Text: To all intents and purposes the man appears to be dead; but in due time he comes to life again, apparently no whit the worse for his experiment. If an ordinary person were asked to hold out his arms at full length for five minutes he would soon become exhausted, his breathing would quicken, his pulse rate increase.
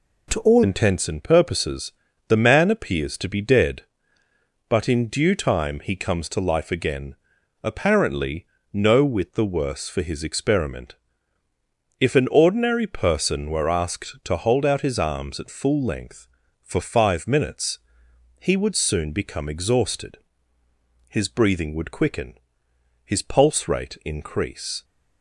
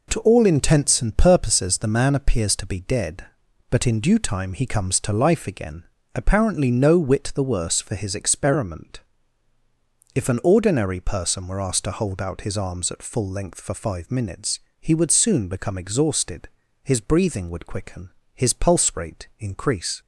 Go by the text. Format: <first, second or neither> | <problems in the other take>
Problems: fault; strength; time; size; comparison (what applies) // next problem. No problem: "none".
second | changes voice at "intents"; from 0.6 s on; 24.2 s long // pauses between "purposes" and "the"; slight; at 1.9 s; 0.36 s long // pauses between "apparently" and "no"; slight; at 8.4 s; 0.28 s long // pauses between "minutes" and "he"; noticeable; at 17.7 s; 0.64 s long; slight in the second